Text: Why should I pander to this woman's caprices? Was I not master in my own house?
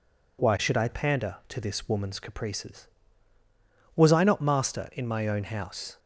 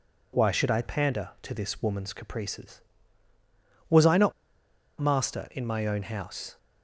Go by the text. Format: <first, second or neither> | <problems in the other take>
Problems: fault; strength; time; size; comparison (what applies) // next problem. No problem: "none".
first | pauses between "not" and "master"; noticeable; at 4.3 s; 0.66 s long